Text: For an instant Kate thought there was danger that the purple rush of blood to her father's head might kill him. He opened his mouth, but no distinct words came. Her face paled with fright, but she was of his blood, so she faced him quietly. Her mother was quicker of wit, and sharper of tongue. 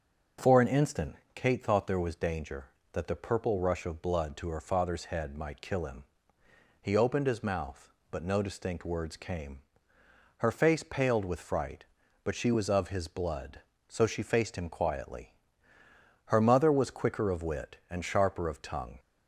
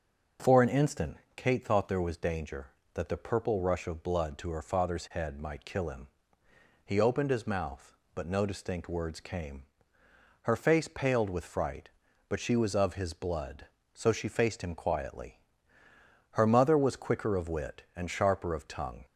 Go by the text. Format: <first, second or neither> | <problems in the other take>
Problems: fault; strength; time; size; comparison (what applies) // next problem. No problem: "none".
neither | starts louder than the rest; the same in both // pauses between "instant" and "Kate"; slight; the same in both